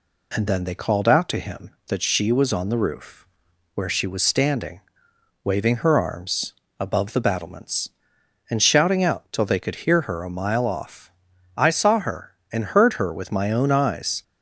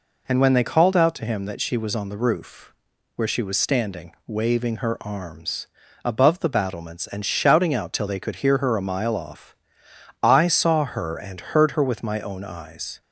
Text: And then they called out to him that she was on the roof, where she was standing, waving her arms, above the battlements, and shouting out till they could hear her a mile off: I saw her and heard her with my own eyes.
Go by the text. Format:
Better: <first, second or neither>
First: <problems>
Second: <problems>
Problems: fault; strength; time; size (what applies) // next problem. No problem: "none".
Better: first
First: none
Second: says "when" for "then"; at 0.4 s